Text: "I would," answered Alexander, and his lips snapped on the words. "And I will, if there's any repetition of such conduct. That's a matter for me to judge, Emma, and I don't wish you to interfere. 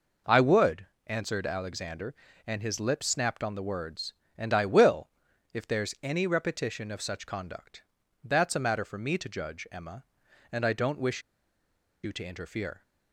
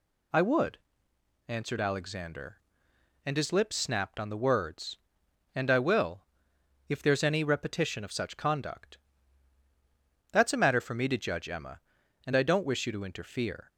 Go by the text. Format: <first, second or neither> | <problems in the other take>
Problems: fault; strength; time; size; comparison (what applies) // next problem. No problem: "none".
second | pauses between "wish" and "you"; noticeable; at 11.2 s; 0.83 s long